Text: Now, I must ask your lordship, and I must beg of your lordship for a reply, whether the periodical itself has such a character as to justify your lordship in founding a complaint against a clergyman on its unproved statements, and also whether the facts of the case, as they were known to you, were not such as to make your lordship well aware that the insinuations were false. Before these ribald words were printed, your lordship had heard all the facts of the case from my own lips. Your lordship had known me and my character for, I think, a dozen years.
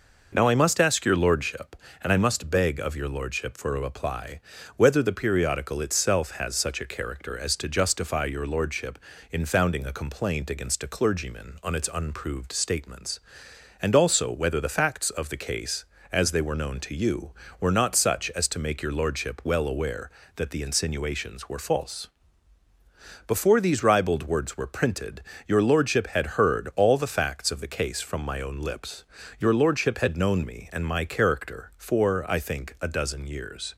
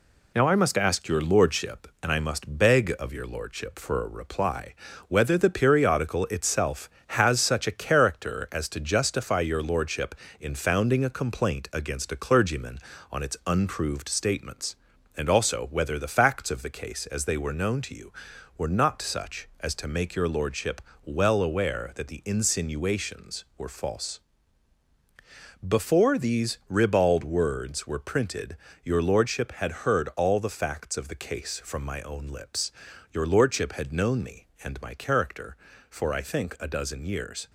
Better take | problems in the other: first | gets quieter; noticeable; throughout; 5 dB // pauses between "lordship" and "well"; slight; at 20.7 s; 0.24 s long

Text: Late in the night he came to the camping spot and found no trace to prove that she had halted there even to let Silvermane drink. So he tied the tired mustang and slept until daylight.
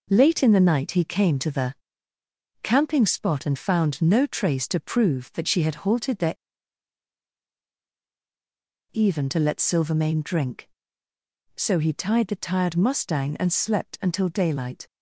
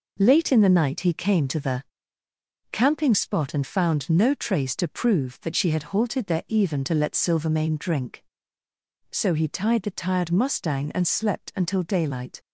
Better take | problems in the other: second | pauses between "the" and "camping"; noticeable; at 1.7 s; 0.88 s long; noticeable in the second // pauses between "there" and "even"; strong; at 6.3 s; 2.5 s long

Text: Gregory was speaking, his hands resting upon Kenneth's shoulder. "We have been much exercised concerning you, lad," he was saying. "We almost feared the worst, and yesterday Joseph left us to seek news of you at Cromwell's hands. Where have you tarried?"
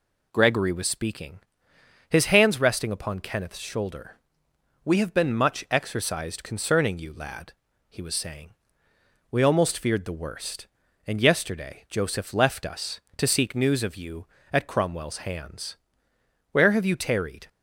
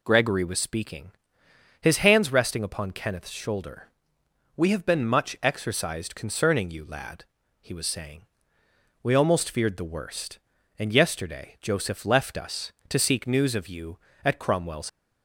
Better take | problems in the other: first | stops before "hands Where have you tarried"; at 14.8 s

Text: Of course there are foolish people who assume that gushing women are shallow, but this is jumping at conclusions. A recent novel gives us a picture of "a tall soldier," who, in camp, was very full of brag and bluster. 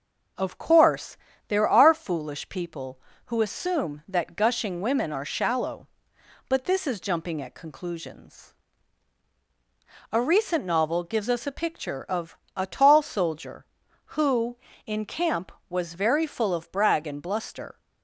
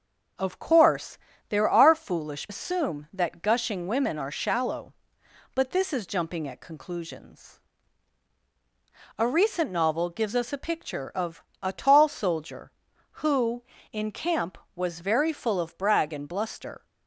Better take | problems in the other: first | starts louder than the rest; until 1.7 s; 6.5 dB // pauses between "course" and "there"; slight; at 1.1 s; 0.32 s long; slight in the first // skips "people who"; at 2.4 s // pauses between "of" and "a"; slight; at 11.4 s; 0.18 s long; slight in the first

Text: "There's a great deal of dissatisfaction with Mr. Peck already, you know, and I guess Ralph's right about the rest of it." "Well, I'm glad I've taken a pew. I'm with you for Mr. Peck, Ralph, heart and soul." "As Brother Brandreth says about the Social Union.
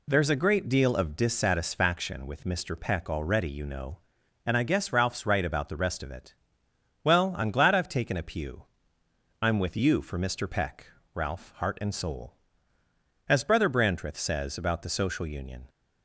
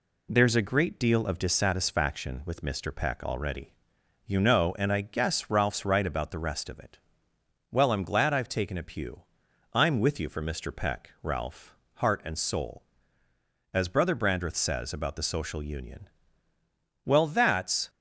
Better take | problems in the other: first | goes on to say "Well that's"; noticeable; from 17.0 s on; 0.84 s long

